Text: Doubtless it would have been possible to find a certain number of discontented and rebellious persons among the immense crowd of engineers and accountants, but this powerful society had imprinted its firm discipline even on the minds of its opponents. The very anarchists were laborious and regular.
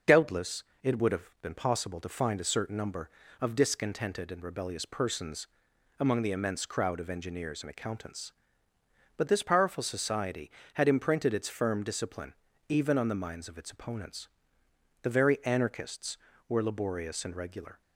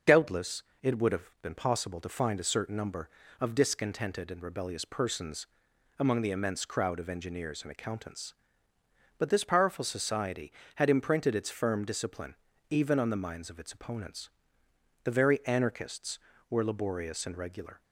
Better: neither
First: starts louder than the rest; until 1.2 s; 6.5 dB // pauses between "Doubtless" and "it"; slight; at 0.6 s; 0.18 s long // pauses between "persons" and "among"; noticeable; at 5.4 s; 0.50 s long // pauses between "discipline" and "even"; slight; at 12.3 s; 0.34 s long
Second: starts louder than the rest; until 1.2 s; 6.5 dB // pauses between "Doubtless" and "it"; slight; at 0.6 s; 0.18 s long // pauses between "persons" and "among"; noticeable; at 5.4 s; 0.50 s long // pauses between "discipline" and "even"; slight; at 12.3 s; 0.34 s long

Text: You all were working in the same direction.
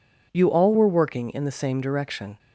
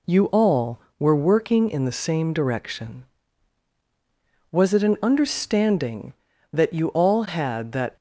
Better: first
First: none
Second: goes on to say "Was it an understanding that you all had that"; strong; from 4.5 s on; 3.4 s long

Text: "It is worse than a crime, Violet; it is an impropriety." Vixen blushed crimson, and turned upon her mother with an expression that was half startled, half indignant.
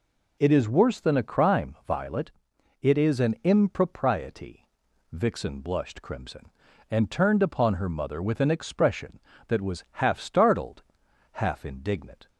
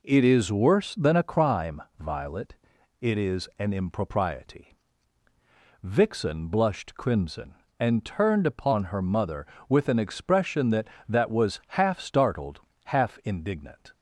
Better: first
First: none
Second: says "that" twice; at 11.0 s

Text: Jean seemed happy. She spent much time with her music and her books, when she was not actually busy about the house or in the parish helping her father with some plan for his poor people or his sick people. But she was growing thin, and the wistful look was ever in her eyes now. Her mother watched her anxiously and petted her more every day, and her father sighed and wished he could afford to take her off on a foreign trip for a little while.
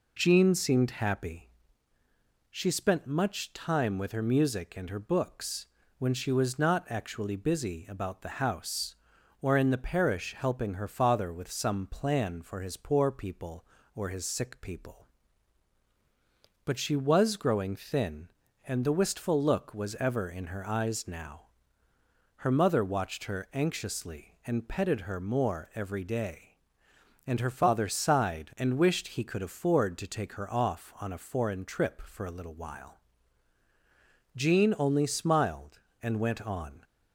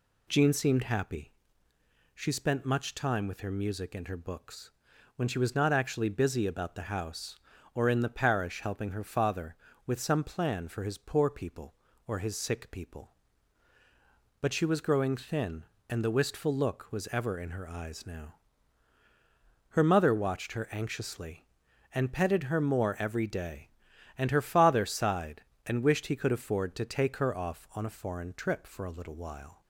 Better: second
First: goes on to say "Jean only smiled and went on"; strong; from 34.3 s on; 2.4 s long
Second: none

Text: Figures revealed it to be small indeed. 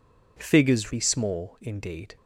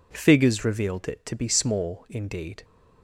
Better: second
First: skips "revealed it to"; at 0.9 s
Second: none

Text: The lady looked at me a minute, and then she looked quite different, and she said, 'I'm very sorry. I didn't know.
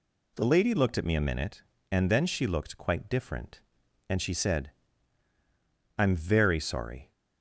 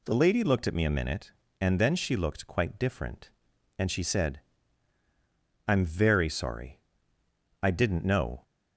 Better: second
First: stops before "I didn't know"; at 7.1 s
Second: none

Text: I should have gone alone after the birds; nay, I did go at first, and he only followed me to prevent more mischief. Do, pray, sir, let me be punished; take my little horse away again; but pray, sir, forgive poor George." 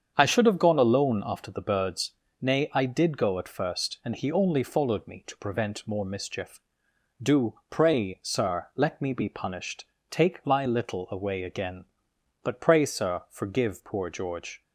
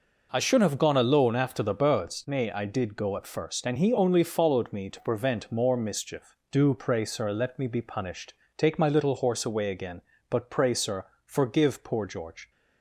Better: second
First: starts louder than the rest; strong; until 1.1 s; 7.5 dB // skips "horse"; at 11.0 s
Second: none

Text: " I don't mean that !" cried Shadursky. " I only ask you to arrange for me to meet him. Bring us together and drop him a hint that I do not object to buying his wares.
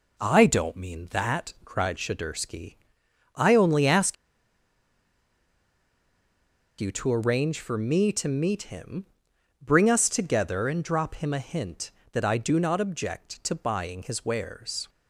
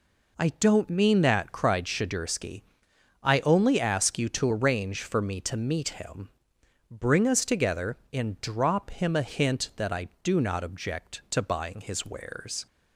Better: second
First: pauses between "ask" and "you"; strong; at 4.1 s; 2.6 s long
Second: none

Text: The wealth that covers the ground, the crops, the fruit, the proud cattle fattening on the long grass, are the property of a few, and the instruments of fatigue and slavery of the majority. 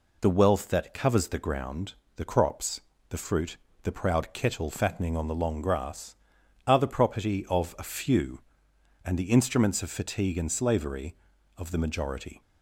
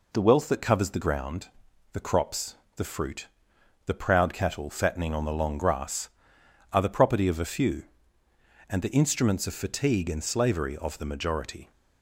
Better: second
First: says "kettle" for "cattle"; at 4.3 s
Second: none

